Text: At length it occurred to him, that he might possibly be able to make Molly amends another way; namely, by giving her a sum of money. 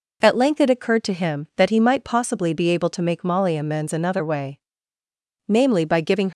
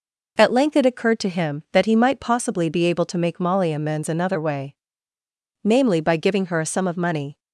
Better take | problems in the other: second | stops before "her a sum of money"; at 6.3 s

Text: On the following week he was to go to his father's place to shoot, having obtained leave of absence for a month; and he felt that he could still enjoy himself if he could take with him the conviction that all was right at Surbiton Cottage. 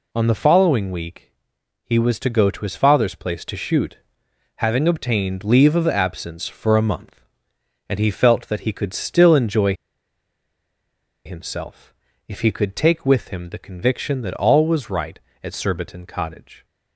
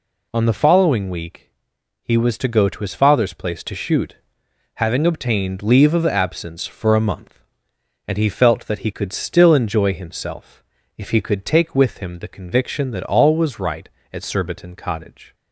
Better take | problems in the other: second | pauses between "week" and "he"; noticeable; at 1.3 s; 0.54 s long; noticeable in the second // pauses between "enjoy" and "himself"; strong; at 9.7 s; 1.5 s long // pauses between "himself" and "if"; slight; at 11.9 s; 0.34 s long; slight in the second

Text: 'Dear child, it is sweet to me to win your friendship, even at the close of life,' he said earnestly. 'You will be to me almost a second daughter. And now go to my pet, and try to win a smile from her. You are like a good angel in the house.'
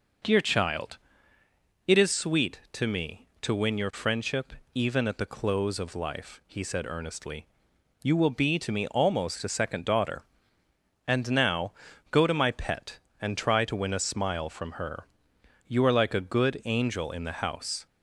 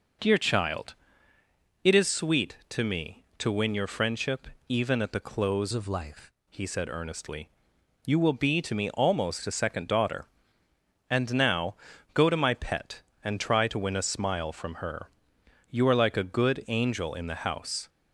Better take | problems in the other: first | changes voice from "of" to "life"; from 5.7 to 6.3 s; 0.6 s long // pauses between "now" and "go"; slight; at 11.7 s; 0.36 s long; slight in the first

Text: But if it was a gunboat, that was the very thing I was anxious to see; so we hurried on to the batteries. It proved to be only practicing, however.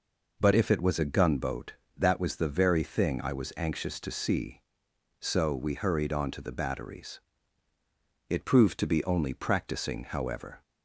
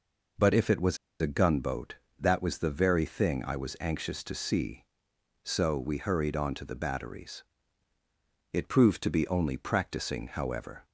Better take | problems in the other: first | pauses between "was" and "a"; slight; at 0.9 s; 0.23 s long

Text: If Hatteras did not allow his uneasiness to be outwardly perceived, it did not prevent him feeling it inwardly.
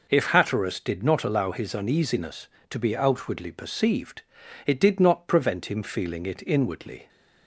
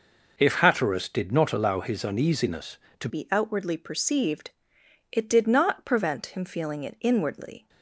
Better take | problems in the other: first | changes voice at "be"; from 3.0 s on; 4.6 s long

